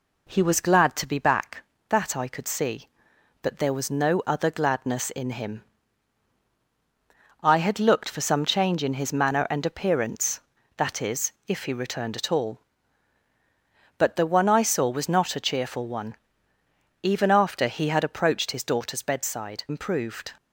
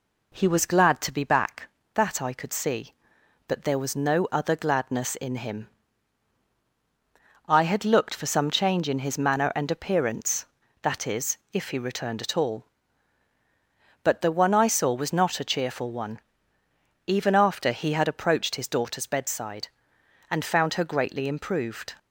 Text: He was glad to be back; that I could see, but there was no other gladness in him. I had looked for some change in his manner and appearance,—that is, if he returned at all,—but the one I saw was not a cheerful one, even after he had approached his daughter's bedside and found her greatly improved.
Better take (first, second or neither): second